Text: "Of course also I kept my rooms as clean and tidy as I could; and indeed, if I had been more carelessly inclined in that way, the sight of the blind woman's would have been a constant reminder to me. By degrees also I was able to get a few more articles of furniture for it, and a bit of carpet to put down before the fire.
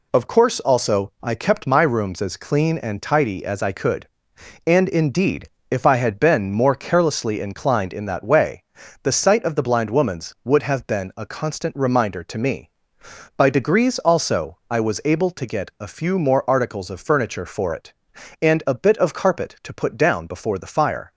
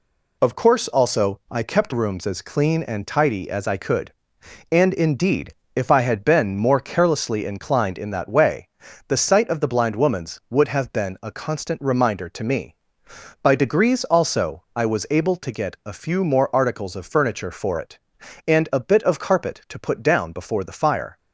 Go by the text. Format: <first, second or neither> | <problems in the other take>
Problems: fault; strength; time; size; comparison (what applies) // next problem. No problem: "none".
first | skips "my"; at 1.9 s